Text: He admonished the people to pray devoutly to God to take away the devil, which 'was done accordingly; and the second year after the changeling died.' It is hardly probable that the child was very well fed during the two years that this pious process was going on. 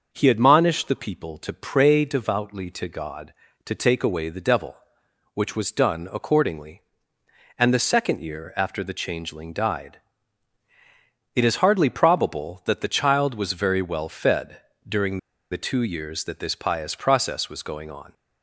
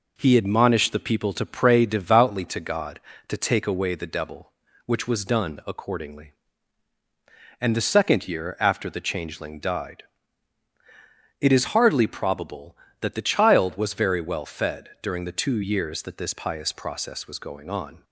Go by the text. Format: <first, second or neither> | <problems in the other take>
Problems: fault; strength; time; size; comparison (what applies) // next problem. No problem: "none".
second | starts louder than the rest; until 1.1 s; 6 dB // pauses between "fed" and "during"; slight; at 14.6 s; 0.26 s long // pauses between "during" and "the"; slight; at 15.1 s; 0.32 s long